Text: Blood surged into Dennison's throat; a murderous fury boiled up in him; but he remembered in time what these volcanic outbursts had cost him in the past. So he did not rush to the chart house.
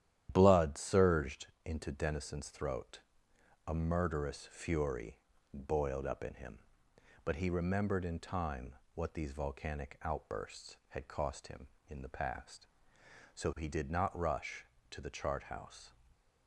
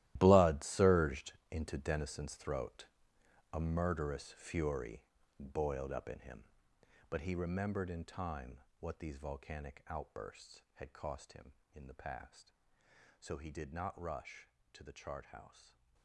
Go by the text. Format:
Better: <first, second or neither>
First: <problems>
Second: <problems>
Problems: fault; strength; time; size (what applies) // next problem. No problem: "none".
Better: first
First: starts louder than the rest; strong; until 1.3 s; 11 dB // pauses between "surged" and "into"; slight; at 1.4 s; 0.18 s long // pauses between "fury" and "boiled"; slight; at 5.1 s; 0.34 s long // pauses between "time" and "what"; slight; at 8.7 s; 0.20 s long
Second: gets quieter; strong; throughout; 15 dB // starts louder than the rest; strong; until 1.1 s; 14.5 dB // pauses between "surged" and "into"; slight; at 1.3 s; 0.18 s long // pauses between "fury" and "boiled"; slight; at 5.0 s; 0.34 s long // pauses between "time" and "what"; slight; at 8.5 s; 0.20 s long